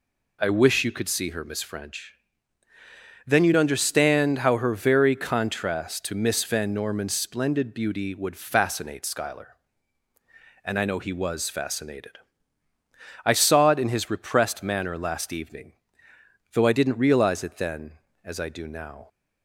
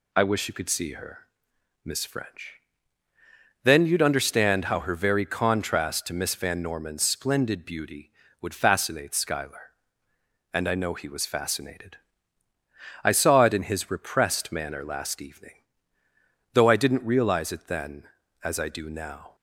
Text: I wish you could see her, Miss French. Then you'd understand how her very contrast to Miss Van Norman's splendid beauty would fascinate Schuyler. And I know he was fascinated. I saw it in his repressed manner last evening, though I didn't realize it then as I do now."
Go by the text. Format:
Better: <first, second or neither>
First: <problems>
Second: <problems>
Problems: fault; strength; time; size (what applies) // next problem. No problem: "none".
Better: neither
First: none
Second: none